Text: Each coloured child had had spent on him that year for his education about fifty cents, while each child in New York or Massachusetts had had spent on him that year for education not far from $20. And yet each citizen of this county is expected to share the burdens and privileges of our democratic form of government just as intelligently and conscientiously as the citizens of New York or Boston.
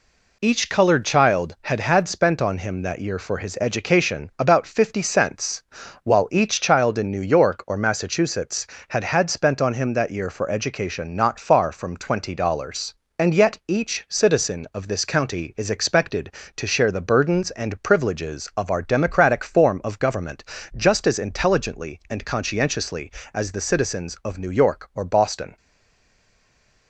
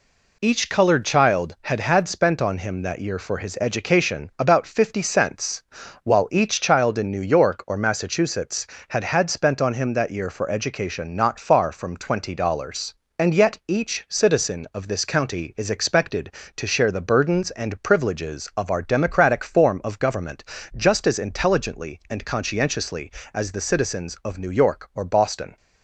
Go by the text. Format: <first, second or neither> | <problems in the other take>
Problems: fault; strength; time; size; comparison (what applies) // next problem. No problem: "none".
second | pauses between "government" and "just"; slight; at 20.4 s; 0.32 s long; slight in the second // stays silent after the last word; noticeable; from 25.5 s on; 1.3 s long